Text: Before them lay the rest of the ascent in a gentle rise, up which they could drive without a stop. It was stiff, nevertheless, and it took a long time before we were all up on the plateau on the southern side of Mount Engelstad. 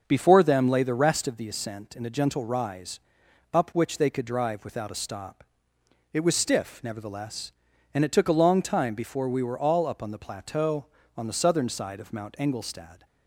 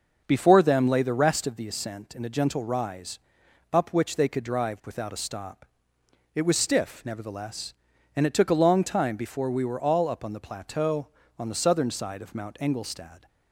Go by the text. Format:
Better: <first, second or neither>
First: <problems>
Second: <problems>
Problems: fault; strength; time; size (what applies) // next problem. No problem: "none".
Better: neither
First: starts louder than the rest; noticeable; until 1.0 s; 6 dB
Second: starts louder than the rest; noticeable; until 1.2 s; 6 dB